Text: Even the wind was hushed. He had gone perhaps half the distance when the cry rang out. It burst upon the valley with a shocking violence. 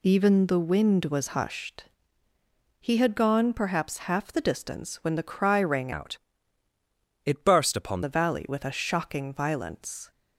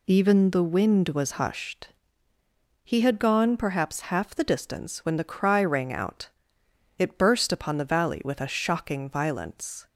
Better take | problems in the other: second | changes voice from "out" to "upon"; from 5.9 to 8.0 s; 2.1 s long

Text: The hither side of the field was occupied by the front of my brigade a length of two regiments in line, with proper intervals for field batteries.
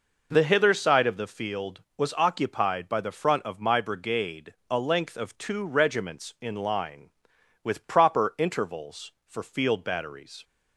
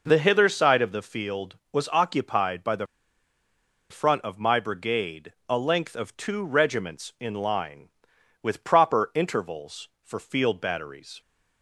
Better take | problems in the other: first | pauses between "the" and "front"; at 2.8 s; 1.0 s long // pauses between "brigade" and "a"; slight; at 5.3 s; 0.16 s long; slight in the first

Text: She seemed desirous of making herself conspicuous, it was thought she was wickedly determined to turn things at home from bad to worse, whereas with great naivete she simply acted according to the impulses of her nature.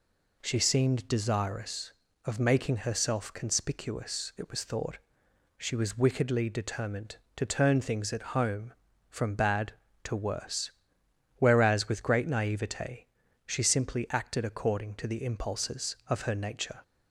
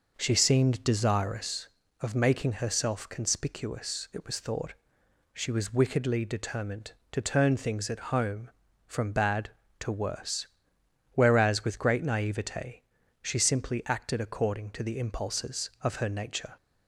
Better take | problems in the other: first | starts louder than the rest; noticeable; until 1.8 s; 5.5 dB // pauses between "thought" and "she"; noticeable; at 4.7 s; 0.58 s long; noticeable in the first // pauses between "naivete" and "she"; at 12.8 s; 0.38 s long; also in the first

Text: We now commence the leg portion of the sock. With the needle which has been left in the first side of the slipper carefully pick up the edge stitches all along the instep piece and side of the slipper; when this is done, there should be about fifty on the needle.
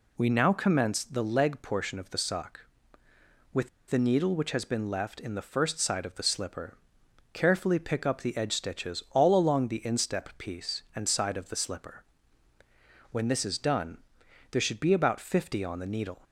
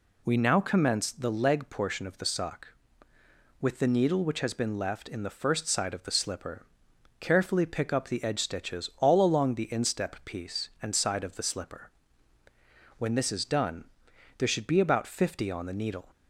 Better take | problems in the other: second | pauses between "With" and "the"; slight; at 3.6 s; 0.21 s long // pauses between "slipper" and "carefully"; noticeable; at 6.7 s; 0.58 s long; noticeable in the second

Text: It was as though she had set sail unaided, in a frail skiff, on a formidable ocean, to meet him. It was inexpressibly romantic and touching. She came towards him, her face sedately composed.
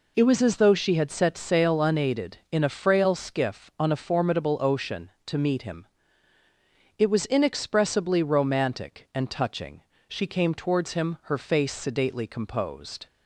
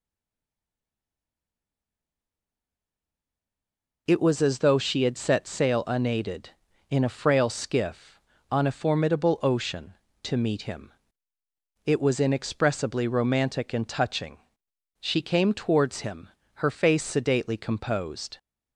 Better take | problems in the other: first | stays silent before the first word; strong; until 4.0 s; 4.0 s long

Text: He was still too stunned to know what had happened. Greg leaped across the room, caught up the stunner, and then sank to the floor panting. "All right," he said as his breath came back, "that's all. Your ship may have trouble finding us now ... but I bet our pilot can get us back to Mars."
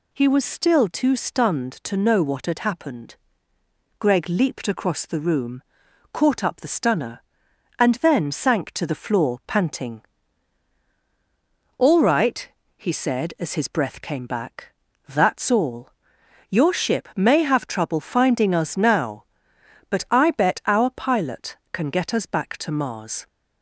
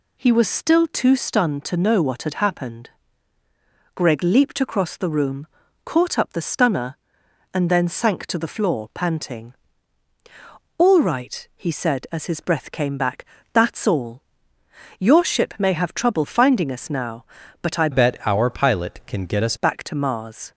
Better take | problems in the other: first | changes voice from "bet" to "us"; from 17.9 to 19.5 s; 1.6 s long

